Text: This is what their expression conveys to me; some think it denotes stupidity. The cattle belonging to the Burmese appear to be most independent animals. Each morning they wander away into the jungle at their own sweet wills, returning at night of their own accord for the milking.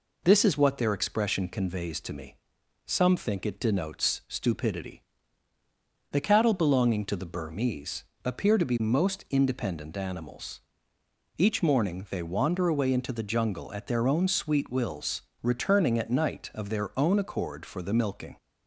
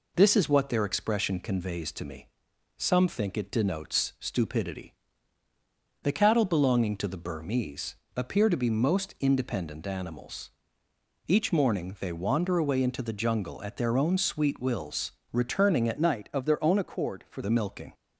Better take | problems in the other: first | pauses between "Burmese" and "appear"; slight; at 7.9 s; 0.18 s long; slight in the first // changes voice from "night" to "for"; from 15.9 to 17.4 s; 1.5 s long

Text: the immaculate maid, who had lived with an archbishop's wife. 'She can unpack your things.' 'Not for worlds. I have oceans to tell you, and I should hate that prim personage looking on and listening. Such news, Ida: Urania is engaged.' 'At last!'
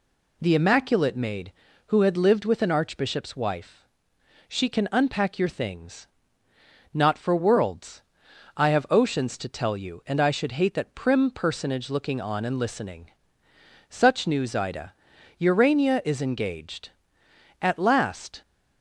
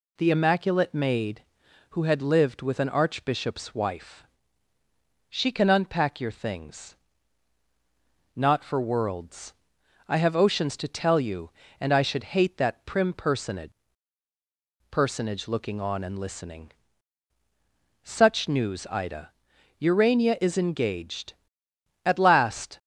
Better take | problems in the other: first | says "personage" twice; at 14.9 s

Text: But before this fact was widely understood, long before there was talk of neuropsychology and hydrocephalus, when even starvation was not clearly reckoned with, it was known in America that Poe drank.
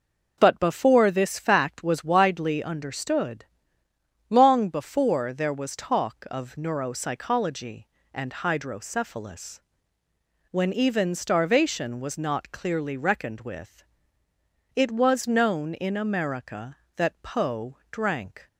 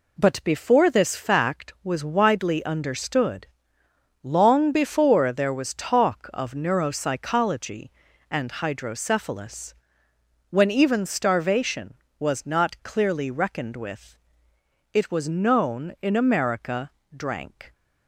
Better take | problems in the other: first | skips "that Poe"; at 17.0 s

